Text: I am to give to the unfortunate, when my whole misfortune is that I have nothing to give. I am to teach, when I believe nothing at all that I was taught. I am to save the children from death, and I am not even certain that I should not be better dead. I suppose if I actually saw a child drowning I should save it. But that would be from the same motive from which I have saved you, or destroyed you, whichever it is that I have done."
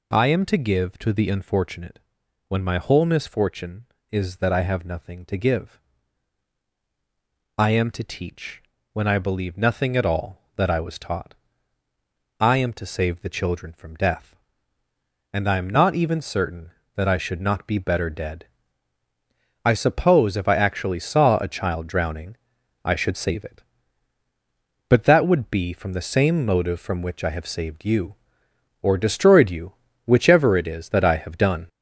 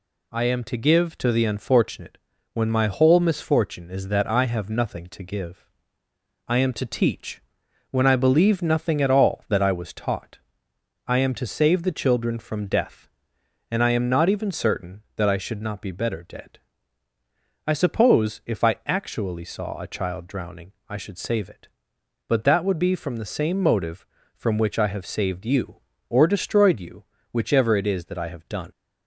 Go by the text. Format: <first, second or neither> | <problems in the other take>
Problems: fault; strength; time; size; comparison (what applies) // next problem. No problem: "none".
second | gets louder; noticeable; throughout; 5 dB // pauses between "drowning" and "I"; noticeable; at 22.3 s; 0.48 s long; slight in the second